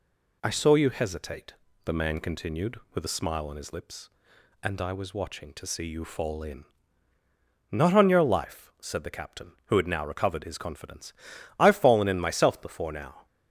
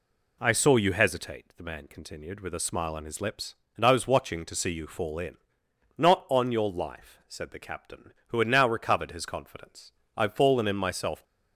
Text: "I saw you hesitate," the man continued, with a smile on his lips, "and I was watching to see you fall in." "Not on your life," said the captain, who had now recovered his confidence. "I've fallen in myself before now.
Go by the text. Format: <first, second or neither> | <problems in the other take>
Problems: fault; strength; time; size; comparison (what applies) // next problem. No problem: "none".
first | stops before "before now"; at 11.2 s